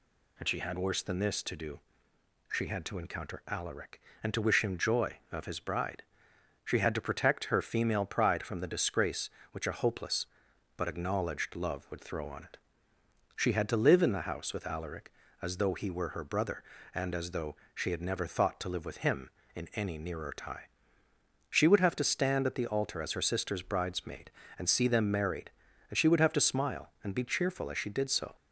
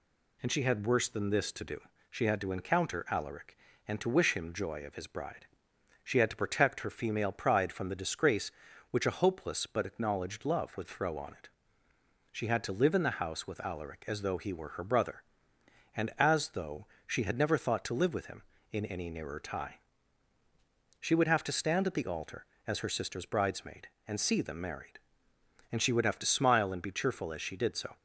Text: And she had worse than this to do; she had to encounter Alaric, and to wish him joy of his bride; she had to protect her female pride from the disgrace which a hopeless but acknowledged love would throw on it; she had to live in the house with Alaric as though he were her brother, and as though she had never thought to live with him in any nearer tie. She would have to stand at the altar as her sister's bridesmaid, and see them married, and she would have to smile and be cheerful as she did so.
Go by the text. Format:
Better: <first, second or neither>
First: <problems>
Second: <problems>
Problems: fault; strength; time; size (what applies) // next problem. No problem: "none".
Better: neither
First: pauses between "though" and "she"; slight; at 17.5 s; 0.18 s long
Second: pauses between "though" and "she"; slight; at 16.8 s; 0.18 s long